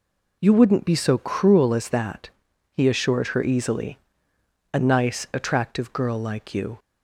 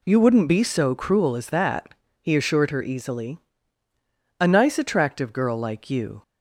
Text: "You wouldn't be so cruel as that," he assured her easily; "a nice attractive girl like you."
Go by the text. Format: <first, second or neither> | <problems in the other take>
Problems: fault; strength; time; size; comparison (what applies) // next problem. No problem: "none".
neither | none